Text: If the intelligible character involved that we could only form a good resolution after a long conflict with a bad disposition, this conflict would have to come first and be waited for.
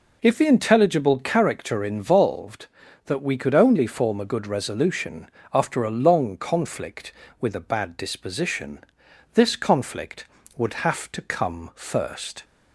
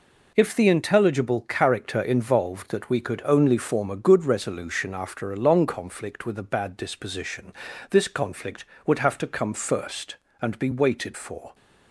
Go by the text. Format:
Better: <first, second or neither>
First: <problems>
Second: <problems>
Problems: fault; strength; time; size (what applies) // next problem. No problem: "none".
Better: second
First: pauses between "resolution" and "after"; slight; at 5.2 s; 0.24 s long // stops before "and be waited for"; at 12.4 s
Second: none